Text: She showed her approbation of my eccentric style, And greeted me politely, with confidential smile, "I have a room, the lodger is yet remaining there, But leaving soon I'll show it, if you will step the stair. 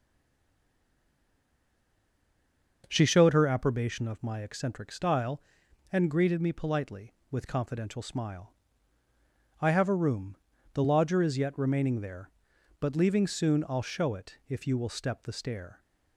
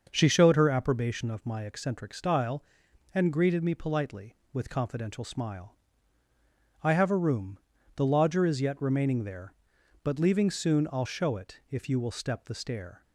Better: second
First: stays silent before the first word; strong; until 2.8 s; 2.8 s long // starts louder than the rest; until 3.8 s; 6.5 dB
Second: starts louder than the rest; until 1.1 s; 6.5 dB

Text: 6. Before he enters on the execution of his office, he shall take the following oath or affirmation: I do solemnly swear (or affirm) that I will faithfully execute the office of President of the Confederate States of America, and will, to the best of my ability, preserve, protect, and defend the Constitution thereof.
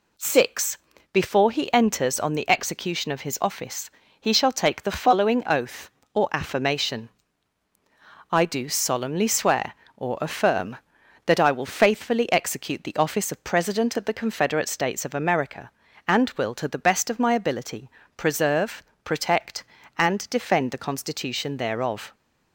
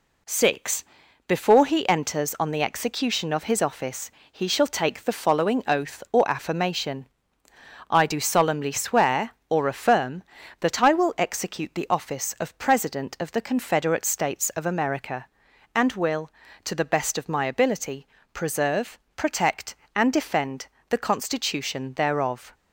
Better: first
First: none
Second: skips "faithfully"; at 11.1 s // pauses between "defend" and "the"; slight; at 20.6 s; 0.20 s long

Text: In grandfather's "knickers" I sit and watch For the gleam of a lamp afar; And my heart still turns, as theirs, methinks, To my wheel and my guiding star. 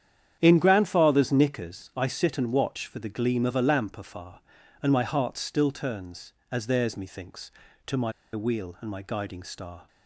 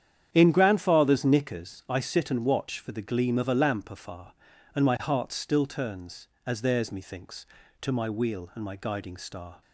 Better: second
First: starts louder than the rest; strong; until 1.4 s; 9.5 dB // pauses between "my" and "wheel"; slight; at 8.1 s; 0.22 s long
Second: starts louder than the rest; strong; until 1.3 s; 9.5 dB

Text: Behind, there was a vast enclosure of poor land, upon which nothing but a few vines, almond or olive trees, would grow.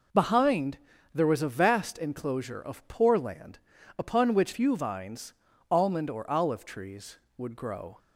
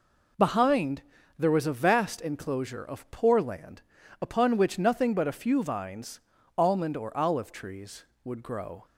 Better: second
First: skips "nothing but a"; at 4.5 s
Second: none

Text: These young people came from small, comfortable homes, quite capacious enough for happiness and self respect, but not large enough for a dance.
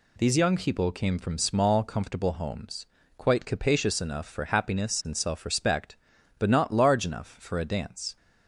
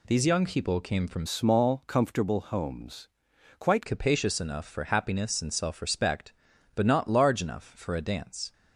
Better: first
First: none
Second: changes voice from "small" to "quite"; from 1.2 to 3.8 s; 2.6 s long

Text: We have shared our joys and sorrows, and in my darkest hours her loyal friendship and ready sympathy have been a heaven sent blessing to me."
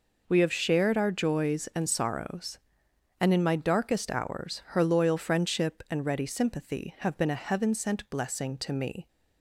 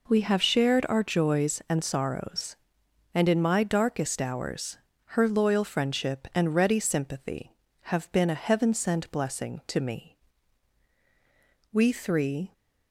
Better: first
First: none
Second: pauses between "hours" and "her"; slight; at 4.7 s; 0.32 s long // goes on to say "We three"; noticeable; from 11.7 s on; 0.80 s long

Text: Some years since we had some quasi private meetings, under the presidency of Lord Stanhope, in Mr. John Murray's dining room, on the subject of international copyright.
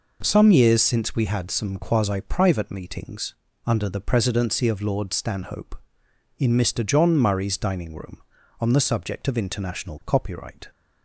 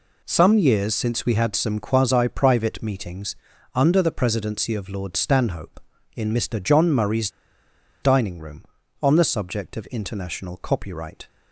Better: first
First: none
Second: pauses between "Murray's" and "dining"; noticeable; at 7.2 s; 0.74 s long

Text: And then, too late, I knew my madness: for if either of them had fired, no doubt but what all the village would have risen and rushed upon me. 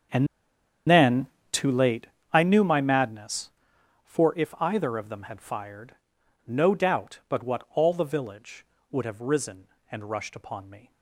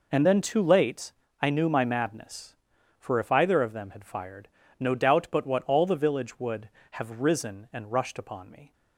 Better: second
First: starts louder than the rest; strong; until 1.9 s; 7.5 dB // pauses between "And" and "then"; noticeable; at 0.2 s; 0.62 s long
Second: none

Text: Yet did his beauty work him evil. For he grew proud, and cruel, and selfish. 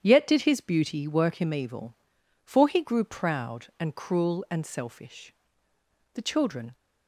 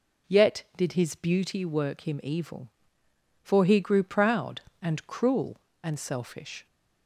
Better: second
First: starts louder than the rest; strong; until 1.0 s; 9.5 dB // goes on to say "The children"; from 6.1 s on; 0.60 s long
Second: none

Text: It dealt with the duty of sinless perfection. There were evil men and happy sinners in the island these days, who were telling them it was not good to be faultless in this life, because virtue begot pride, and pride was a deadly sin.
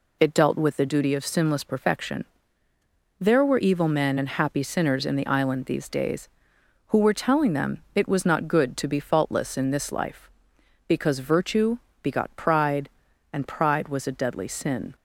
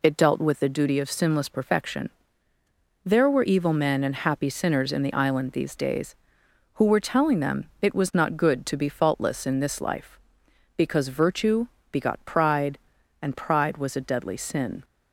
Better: neither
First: pauses between "virtue" and "begot"; slight; at 11.7 s; 0.24 s long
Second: pauses between "virtue" and "begot"; slight; at 11.6 s; 0.24 s long

